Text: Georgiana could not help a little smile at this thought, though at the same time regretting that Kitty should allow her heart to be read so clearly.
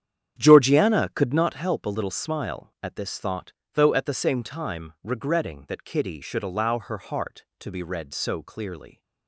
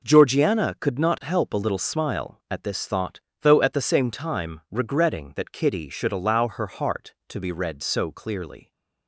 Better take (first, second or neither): second